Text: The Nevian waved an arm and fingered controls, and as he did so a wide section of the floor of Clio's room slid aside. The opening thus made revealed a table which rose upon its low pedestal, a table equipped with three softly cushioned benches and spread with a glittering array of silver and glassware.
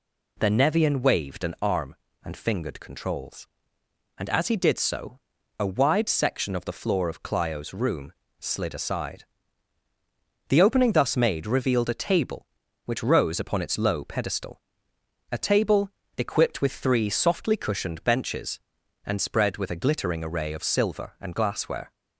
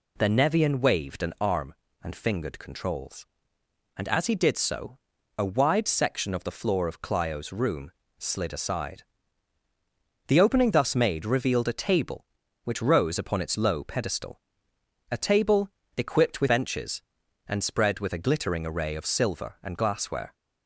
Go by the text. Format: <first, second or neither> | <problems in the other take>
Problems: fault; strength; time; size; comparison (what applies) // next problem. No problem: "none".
first | pauses between "so" and "a"; at 4.9 s; 0.42 s long; also in the first // pauses between "room" and "slid"; slight; at 7.9 s; 0.26 s long; slight in the first // pauses between "table" and "equipped"; slight; at 15.6 s; 0.28 s long; slight in the first // skips "three softly cushioned"; at 16.4 s